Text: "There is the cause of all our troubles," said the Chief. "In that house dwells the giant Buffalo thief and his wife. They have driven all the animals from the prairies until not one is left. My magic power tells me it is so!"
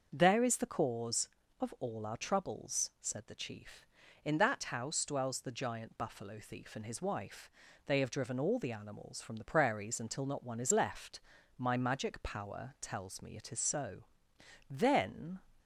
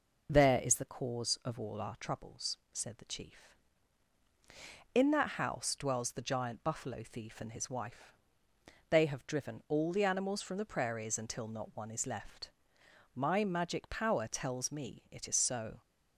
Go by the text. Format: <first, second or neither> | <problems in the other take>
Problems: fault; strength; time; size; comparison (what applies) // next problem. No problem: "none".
second | starts louder than the rest; until 1.1 s; 6.5 dB // goes on to say "Then"; noticeable; from 14.7 s on; 0.70 s long